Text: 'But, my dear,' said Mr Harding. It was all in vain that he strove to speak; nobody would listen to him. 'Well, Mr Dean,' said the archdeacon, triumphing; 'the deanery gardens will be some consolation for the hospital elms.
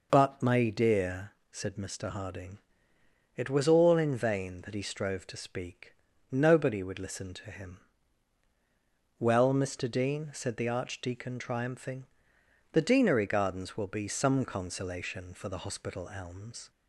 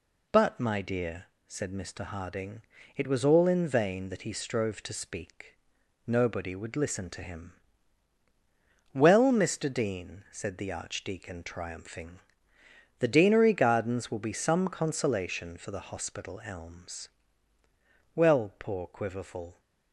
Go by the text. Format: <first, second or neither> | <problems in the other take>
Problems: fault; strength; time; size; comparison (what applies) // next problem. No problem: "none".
first | goes on to say "Well poor Quiverful"; from 18.1 s on; 1.4 s long